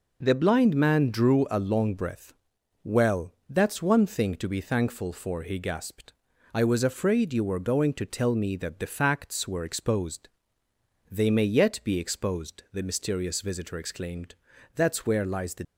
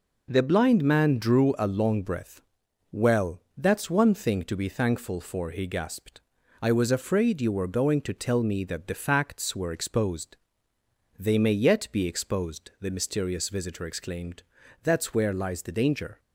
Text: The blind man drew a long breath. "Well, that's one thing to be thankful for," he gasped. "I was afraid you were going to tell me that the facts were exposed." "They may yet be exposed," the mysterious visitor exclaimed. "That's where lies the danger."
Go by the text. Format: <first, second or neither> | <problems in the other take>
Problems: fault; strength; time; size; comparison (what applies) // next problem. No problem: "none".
second | stops before "danger"; at 15.6 s